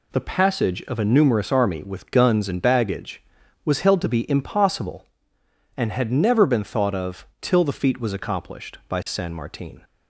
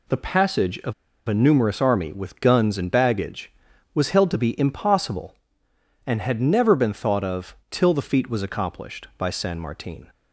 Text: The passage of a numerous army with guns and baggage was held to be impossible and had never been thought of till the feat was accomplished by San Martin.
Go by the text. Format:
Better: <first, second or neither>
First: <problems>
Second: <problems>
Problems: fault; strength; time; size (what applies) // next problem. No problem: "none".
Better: first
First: none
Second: pauses between "of" and "a"; slight; at 0.9 s; 0.34 s long